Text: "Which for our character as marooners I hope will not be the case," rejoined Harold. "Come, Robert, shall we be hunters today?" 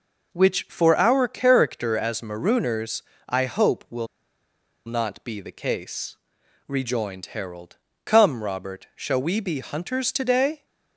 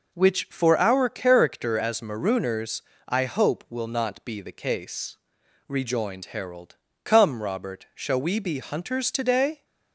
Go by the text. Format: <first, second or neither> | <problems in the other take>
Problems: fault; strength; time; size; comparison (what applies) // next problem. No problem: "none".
second | pauses between "marooners" and "I"; slight; at 3.0 s; 0.26 s long; slight in the second // pauses between "will" and "not"; noticeable; at 4.0 s; 0.80 s long